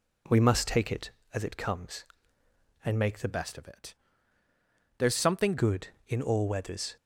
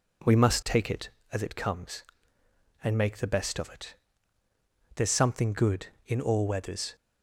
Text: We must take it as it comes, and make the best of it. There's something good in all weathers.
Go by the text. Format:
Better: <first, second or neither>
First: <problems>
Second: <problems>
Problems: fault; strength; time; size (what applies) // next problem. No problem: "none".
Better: second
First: changes voice from "best" to "something"; from 3.2 to 5.5 s; 2.3 s long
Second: none